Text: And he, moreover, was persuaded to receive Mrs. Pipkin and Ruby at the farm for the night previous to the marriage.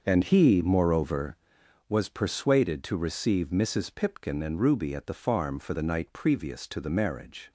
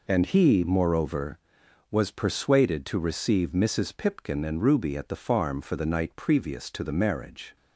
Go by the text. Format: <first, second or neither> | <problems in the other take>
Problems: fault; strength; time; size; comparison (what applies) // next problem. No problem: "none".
second | starts louder than the rest; until 1.6 s; 6.5 dB